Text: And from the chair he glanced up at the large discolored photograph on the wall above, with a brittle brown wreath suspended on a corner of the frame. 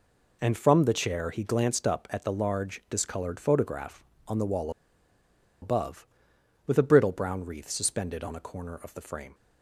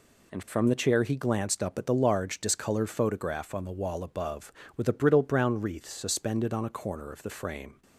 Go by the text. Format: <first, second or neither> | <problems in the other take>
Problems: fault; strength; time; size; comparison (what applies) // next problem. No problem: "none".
second | pauses between "wall" and "above"; noticeable; at 4.7 s; 0.91 s long